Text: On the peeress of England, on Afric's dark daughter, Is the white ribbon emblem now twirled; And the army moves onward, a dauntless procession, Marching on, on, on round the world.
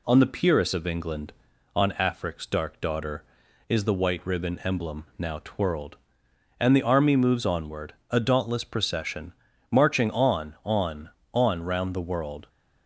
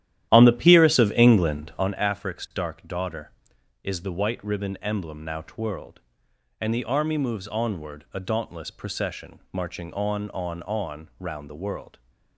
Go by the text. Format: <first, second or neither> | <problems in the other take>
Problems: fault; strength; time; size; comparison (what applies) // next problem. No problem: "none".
first | starts louder than the rest; strong; until 1.9 s; 12 dB